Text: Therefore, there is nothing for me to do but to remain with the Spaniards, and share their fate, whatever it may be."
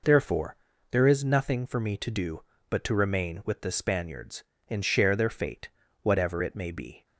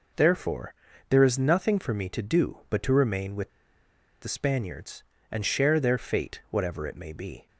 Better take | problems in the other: first | pauses between "with" and "the"; noticeable; at 3.4 s; 0.72 s long

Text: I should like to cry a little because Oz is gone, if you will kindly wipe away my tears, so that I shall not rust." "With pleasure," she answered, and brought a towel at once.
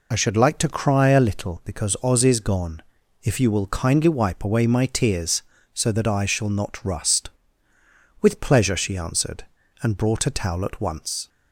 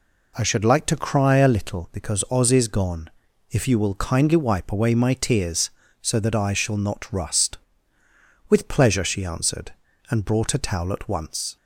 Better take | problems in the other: second | loses the start of "I"; at 0.1 s; 30 ms

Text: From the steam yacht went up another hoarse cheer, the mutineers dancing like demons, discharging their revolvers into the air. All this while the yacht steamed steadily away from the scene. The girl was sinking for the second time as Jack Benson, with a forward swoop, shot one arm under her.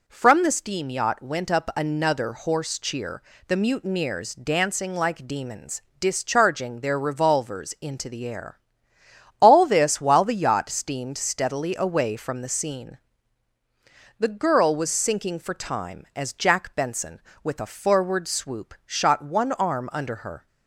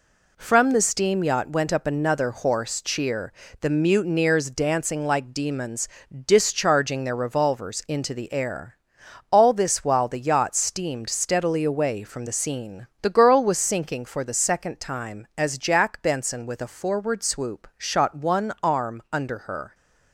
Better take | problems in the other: second | skips "the second"; at 15.5 s

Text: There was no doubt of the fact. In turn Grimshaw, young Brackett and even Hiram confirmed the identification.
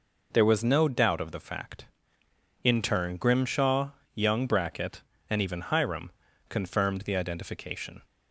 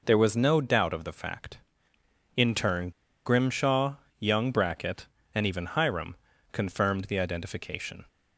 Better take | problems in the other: first | pauses between "turn" and "Grimshaw"; slight; at 2.8 s; 0.35 s long // pauses between "Hiram" and "confirmed"; at 6.1 s; 0.38 s long; also in the first

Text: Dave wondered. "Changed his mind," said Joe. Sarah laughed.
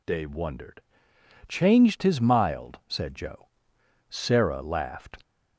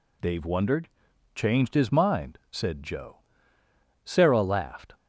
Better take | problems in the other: second | says "mild" for "mind"; at 2.1 s

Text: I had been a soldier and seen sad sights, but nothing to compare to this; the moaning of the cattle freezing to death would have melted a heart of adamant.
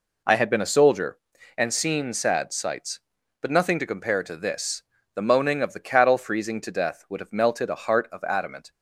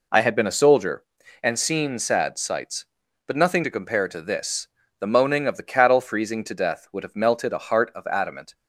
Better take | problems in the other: neither | none

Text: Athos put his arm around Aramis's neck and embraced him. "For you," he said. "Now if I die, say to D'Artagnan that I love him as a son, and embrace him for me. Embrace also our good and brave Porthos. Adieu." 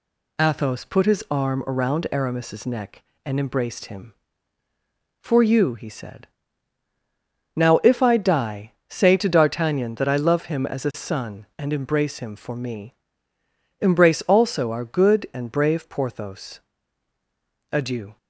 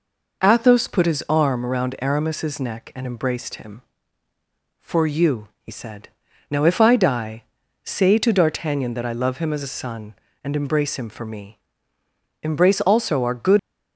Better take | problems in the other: first | stops before "and brave Porthos Adieu"; at 13.5 s

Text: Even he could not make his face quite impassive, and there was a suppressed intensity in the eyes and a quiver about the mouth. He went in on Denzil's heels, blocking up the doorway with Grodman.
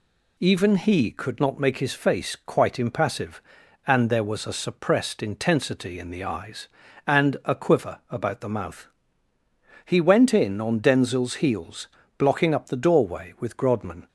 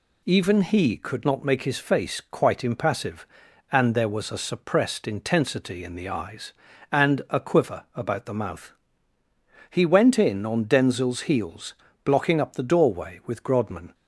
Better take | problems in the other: neither | none

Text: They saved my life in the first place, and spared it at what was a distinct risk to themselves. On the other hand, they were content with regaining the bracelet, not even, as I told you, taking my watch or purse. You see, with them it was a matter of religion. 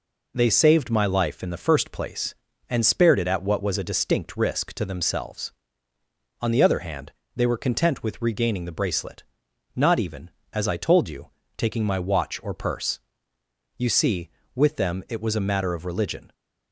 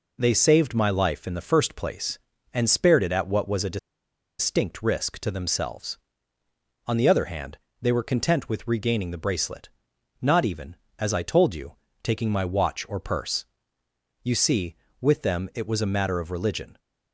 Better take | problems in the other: first | pauses between "a" and "distinct"; noticeable; at 3.7 s; 0.62 s long

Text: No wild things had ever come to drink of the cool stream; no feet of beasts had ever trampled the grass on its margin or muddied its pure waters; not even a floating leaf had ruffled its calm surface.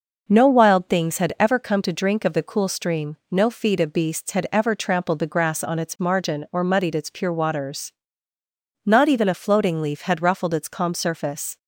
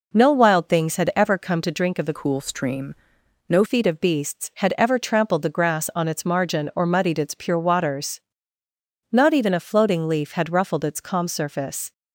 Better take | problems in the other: first | changes voice from "cool" to "no"; from 2.1 to 3.6 s; 1.5 s long

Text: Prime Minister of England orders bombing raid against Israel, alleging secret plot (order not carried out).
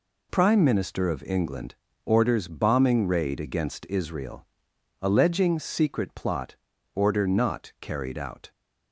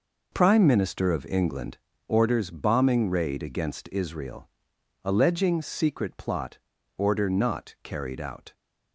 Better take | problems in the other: first | starts louder than the rest; noticeable; until 1.9 s; 5 dB // pauses between "England" and "orders"; slight; at 1.7 s; 0.30 s long; slight in the first

